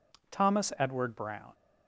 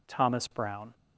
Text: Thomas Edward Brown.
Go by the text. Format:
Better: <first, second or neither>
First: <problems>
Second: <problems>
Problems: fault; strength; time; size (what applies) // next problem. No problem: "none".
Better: first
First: none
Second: skips "Edward"; at 0.4 s